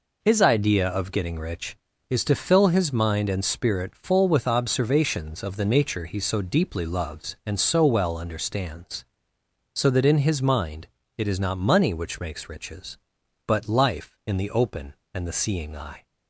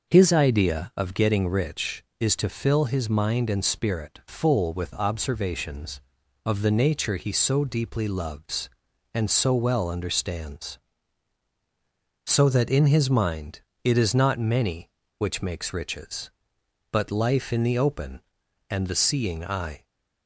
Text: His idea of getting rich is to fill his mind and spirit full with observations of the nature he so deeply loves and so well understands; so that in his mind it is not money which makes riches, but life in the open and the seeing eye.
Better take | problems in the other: first | starts louder than the rest; noticeable; until 1.1 s; 6 dB // pauses between "mind" and "it"; slight; at 13.5 s; 0.24 s long; slight in the first // says "many" for "money"; at 14.3 s

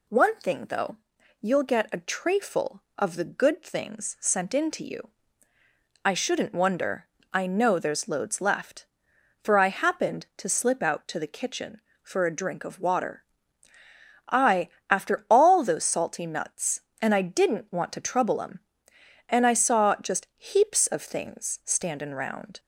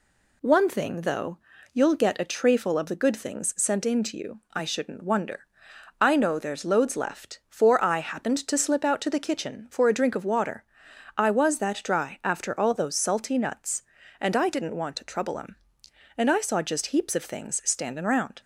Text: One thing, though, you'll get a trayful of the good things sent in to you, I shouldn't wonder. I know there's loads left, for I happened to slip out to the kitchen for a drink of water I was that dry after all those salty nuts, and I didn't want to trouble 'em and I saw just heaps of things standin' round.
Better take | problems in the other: second | pauses between "water" and "I"; at 13.2 s; 1.0 s long; noticeable in the second // skips "was that dry"; at 14.7 s

